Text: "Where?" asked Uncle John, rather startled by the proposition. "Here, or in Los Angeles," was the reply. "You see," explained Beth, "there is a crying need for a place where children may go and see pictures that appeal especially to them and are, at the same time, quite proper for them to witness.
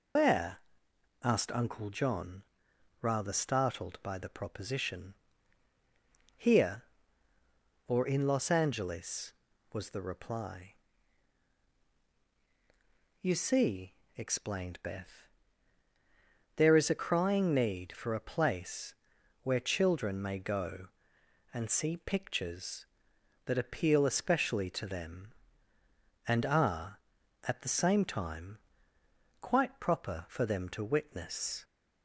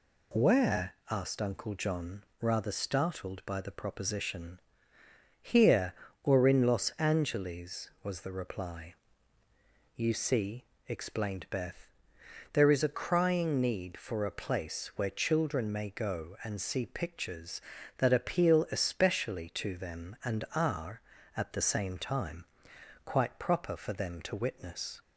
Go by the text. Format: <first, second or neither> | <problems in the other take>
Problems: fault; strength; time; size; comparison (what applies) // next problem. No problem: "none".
second | loses the start of "Where"; at 0.1 s; 160 ms // pauses between "place" and "where"; noticeable; at 18.9 s; 0.48 s long